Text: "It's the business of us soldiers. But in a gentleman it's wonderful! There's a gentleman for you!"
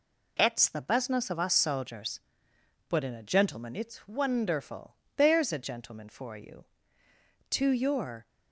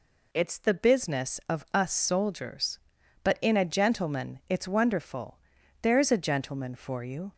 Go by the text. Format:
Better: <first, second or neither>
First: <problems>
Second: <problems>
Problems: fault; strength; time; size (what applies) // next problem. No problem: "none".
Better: second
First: goes on to say "To your"; noticeable; from 7.4 s on; 0.78 s long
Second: none